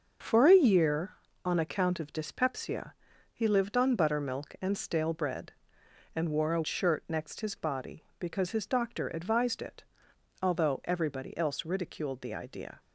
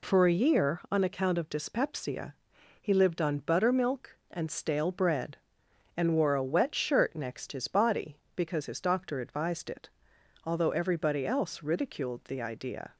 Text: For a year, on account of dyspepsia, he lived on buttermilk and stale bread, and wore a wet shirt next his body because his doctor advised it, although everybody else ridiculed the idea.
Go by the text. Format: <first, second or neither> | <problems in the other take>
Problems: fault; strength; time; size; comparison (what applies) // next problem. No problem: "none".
second | starts louder than the rest; until 1.5 s; 6.5 dB // skips "wet"; at 6.6 s